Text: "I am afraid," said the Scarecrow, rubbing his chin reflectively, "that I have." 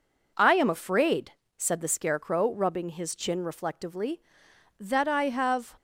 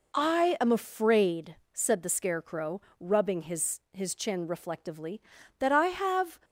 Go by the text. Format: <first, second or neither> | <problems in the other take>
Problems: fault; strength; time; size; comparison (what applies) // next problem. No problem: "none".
first | says "his" twice; at 3.9 s